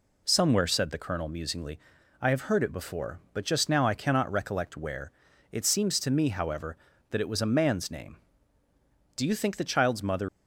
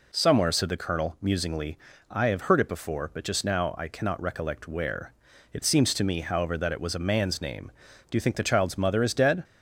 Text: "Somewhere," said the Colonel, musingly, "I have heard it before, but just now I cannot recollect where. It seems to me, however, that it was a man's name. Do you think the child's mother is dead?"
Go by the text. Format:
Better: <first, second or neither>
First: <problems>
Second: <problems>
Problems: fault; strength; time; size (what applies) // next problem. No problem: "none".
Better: second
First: stops before "is dead"; at 10.2 s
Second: none